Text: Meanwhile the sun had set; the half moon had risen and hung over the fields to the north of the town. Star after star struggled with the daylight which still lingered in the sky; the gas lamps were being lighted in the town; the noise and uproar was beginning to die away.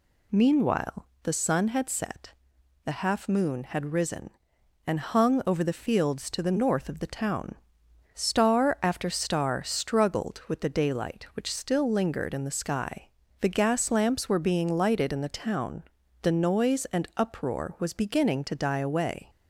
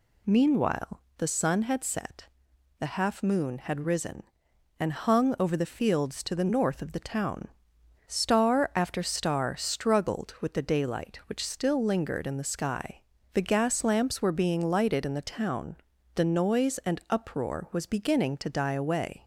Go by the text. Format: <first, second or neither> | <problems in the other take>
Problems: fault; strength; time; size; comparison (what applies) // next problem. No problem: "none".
neither | pauses between "Meanwhile" and "the"; slight; the same in both